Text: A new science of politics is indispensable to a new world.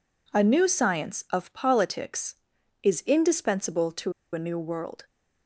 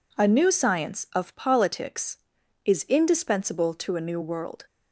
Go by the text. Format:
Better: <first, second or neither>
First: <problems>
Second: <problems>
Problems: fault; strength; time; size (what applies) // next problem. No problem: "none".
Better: second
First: pauses between "to" and "a"; slight; at 4.1 s; 0.21 s long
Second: none